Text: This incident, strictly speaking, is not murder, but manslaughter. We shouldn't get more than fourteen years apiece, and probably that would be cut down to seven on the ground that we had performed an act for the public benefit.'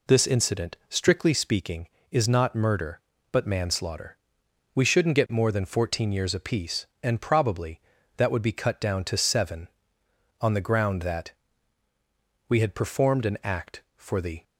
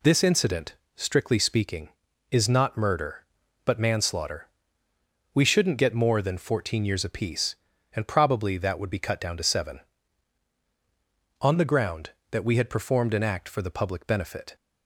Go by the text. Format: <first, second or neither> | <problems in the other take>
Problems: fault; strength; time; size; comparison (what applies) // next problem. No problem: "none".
second | pauses between "that" and "we"; at 11.3 s; 1.1 s long // stops before "public benefit"; at 14.4 s